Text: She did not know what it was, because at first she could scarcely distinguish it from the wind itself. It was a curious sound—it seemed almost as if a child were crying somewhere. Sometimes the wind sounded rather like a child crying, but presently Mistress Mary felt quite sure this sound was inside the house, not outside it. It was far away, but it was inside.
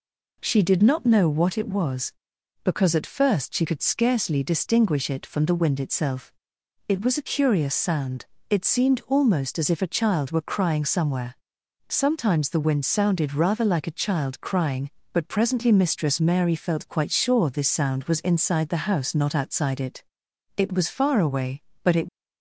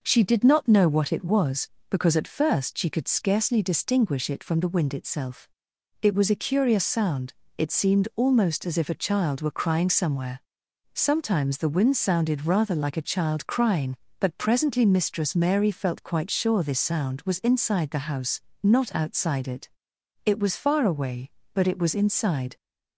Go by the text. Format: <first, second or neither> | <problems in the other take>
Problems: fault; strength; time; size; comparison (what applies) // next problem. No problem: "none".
second | stops before "was inside"; at 22.0 s